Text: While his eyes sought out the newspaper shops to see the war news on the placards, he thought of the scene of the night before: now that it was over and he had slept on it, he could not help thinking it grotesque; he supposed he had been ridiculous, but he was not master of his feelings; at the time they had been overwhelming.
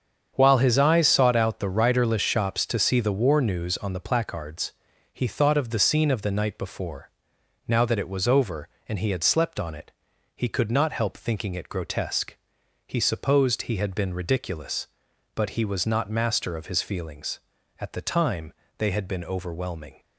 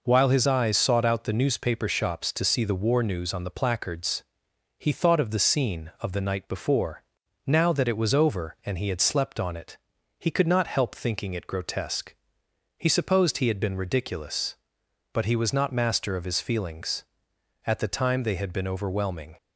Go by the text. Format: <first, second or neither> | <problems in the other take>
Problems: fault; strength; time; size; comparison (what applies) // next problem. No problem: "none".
second | starts louder than the rest; strong; until 1.3 s; 7.5 dB // says "riderless" for "newspaper"; at 1.6 s // pauses between "time" and "they"; slight; at 18.5 s; 0.24 s long